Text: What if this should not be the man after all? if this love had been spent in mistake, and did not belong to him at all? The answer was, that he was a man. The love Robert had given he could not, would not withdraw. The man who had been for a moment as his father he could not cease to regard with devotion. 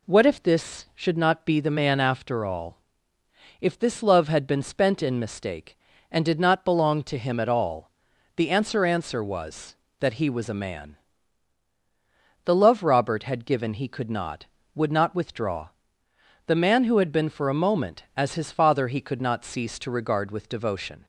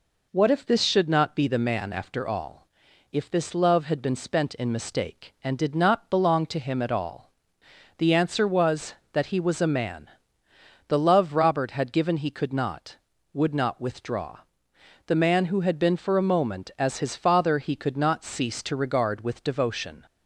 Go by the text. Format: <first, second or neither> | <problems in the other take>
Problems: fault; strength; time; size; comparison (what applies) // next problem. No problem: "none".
second | says "answer" twice; at 8.8 s